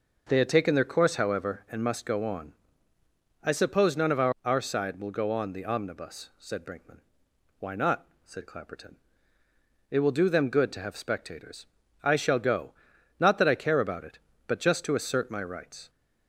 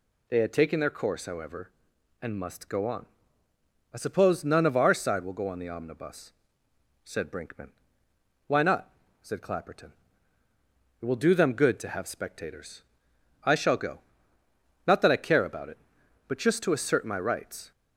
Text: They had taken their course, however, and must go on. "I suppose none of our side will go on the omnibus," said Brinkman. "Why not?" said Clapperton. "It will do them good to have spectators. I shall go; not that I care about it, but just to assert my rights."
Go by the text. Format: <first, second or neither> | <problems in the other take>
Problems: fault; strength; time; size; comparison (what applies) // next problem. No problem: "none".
second | says "our" twice; at 4.4 s